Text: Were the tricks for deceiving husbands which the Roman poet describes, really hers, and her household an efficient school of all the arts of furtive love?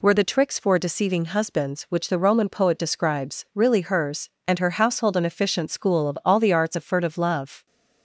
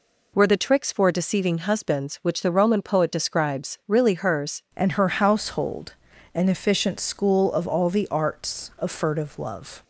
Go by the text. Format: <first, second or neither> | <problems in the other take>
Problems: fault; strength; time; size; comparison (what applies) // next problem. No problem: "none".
first | changes voice at "and"; from 4.7 s on; 5.1 s long // pauses between "household" and "an"; at 5.9 s; 0.42 s long